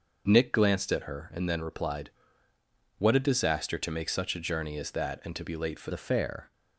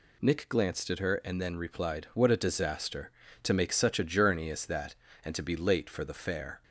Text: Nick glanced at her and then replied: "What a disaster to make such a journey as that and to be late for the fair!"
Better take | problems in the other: second | starts louder than the rest; until 1.2 s; 6.5 dB // changes voice at "the"; from 5.8 s on; 0.7 s long

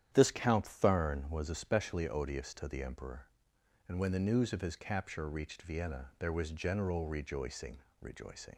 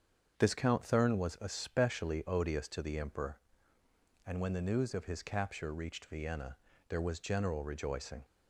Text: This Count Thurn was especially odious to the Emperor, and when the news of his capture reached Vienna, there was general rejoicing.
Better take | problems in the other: second | starts louder than the rest; strong; until 1.1 s; 10 dB; strong in the second // says "rejoicing" twice; at 7.9 s

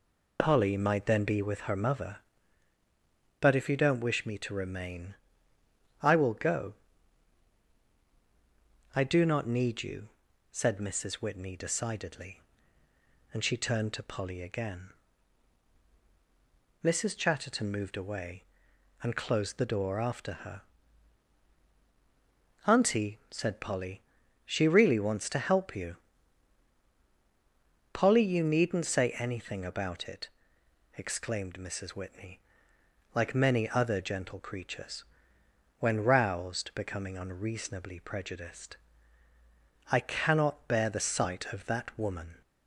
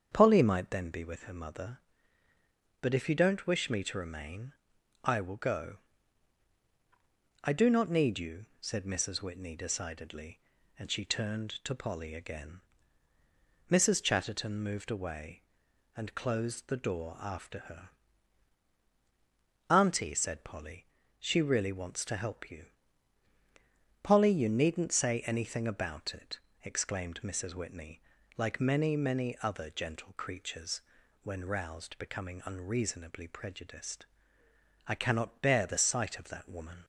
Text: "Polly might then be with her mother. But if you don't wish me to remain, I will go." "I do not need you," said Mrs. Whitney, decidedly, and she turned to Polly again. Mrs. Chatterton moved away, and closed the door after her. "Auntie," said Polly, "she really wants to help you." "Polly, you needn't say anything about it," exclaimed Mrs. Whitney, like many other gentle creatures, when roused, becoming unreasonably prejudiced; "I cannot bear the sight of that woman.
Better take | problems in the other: first | starts louder than the rest; strong; until 1.1 s; 7.5 dB // says "many" twice; at 28.9 s

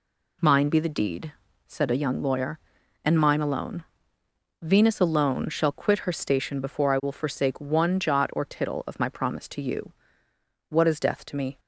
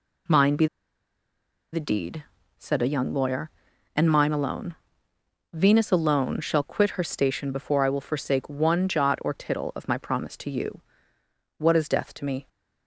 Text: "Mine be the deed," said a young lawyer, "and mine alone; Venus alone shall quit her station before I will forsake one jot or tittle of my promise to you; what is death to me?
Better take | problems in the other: first | pauses between "be" and "the"; at 0.6 s; 1.0 s long

